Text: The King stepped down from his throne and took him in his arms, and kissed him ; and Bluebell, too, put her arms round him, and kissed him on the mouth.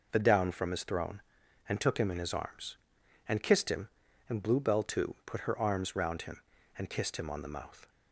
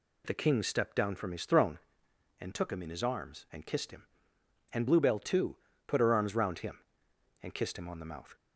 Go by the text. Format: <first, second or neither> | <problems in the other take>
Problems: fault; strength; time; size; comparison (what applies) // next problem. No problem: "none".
second | skips "King stepped"; at 0.1 s